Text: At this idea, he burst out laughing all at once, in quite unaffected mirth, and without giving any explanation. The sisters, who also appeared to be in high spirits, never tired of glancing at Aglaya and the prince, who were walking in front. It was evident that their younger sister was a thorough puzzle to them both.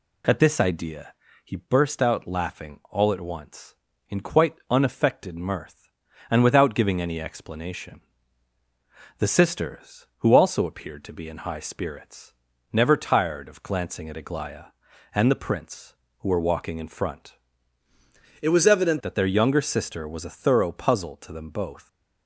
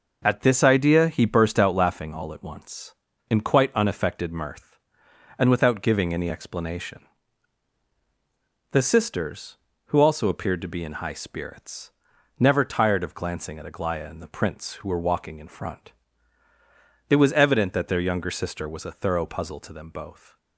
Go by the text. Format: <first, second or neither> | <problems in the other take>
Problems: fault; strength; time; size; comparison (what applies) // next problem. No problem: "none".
second | changes voice from "It" to "evident"; from 18.4 to 19.0 s; 0.6 s long